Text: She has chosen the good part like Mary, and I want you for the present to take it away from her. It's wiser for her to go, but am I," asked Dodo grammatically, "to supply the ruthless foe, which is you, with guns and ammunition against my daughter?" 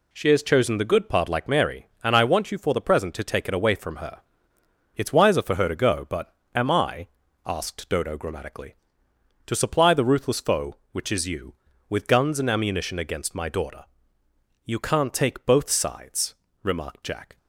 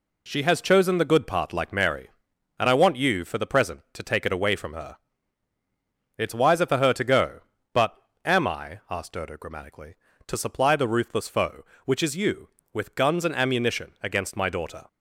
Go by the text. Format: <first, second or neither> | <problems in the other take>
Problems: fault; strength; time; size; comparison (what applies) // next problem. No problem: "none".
second | pauses between "but" and "am"; slight; at 6.3 s; 0.22 s long; slight in the second // goes on to say "You can't take both sides remarked Jack"; strong; from 14.6 s on; 2.7 s long